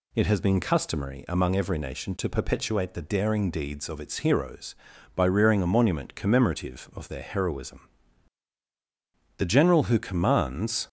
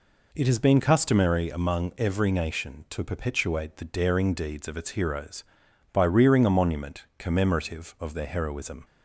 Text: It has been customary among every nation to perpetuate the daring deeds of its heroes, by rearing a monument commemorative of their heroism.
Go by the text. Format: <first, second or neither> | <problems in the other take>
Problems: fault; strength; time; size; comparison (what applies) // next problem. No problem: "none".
second | goes on to say "The general who commands"; from 9.3 s on; 1.5 s long